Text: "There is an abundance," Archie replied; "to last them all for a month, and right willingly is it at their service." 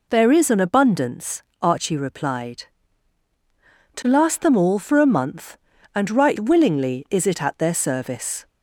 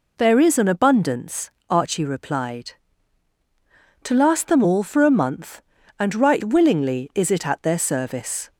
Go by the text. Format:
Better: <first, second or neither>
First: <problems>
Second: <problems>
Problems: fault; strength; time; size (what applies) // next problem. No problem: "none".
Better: neither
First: none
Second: none